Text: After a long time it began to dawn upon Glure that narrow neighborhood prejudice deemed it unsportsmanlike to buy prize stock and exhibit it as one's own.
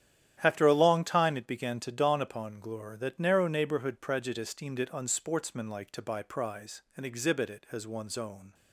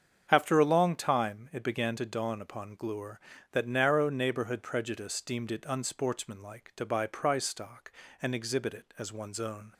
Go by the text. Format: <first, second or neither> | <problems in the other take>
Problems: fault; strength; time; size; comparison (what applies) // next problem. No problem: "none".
second | starts louder than the rest; strong; until 1.4 s; 11 dB; strong in the second // skips "stock"; at 6.8 s